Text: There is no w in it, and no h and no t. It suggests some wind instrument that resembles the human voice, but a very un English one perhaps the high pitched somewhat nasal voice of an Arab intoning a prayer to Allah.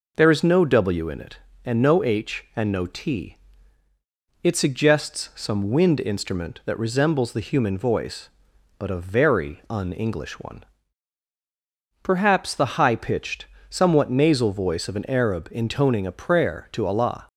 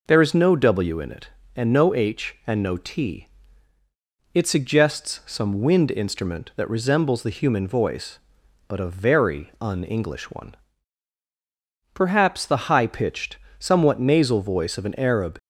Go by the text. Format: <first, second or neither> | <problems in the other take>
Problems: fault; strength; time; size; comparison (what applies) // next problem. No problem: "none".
first | pauses between "one" and "perhaps"; strong; at 10.5 s; 1.3 s long; strong in the first // pauses between "pitched" and "somewhat"; slight; at 13.3 s; 0.22 s long; slight in the first // stops before "intoning a prayer to Allah"; at 15.3 s